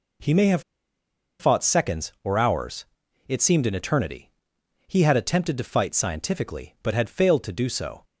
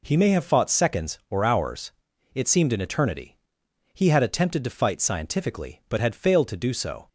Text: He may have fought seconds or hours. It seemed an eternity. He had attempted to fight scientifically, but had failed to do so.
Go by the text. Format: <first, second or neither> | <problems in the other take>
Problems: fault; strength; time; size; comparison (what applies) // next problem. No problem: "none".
second | pauses between "have" and "fought"; noticeable; at 0.6 s; 0.78 s long